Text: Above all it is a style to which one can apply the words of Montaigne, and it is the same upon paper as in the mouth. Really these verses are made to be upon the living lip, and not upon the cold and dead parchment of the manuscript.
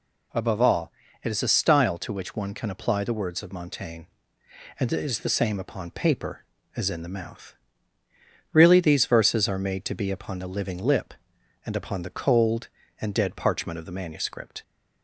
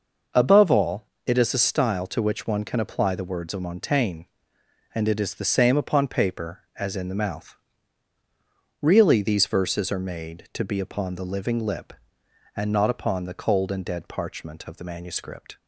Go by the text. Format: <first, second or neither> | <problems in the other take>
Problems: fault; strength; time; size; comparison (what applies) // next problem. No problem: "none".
second | pauses between "all" and "it"; slight; at 0.9 s; 0.30 s long; slight in the second // skips "not"; at 11.7 s